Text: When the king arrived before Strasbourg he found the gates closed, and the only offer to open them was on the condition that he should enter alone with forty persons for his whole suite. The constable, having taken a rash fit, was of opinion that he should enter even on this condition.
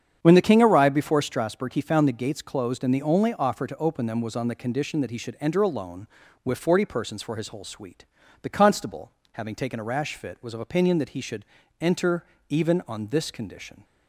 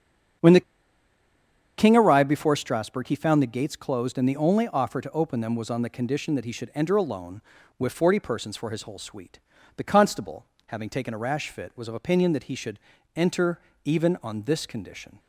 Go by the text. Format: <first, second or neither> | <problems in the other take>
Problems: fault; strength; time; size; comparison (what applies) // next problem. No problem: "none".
first | starts louder than the rest; strong; until 2.5 s; 8 dB; strong in the first // pauses between "the" and "king"; at 0.6 s; 1.1 s long // pauses between "should" and "enter"; slight; at 12.7 s; 0.36 s long; slight in the first // pauses between "enter" and "even"; slight; at 13.5 s; 0.26 s long; slight in the first